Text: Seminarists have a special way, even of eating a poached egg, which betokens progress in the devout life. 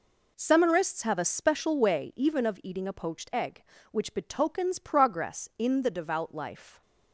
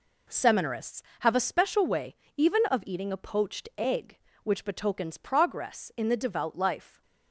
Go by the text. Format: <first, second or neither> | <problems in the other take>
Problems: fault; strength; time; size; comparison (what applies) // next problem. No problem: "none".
neither | none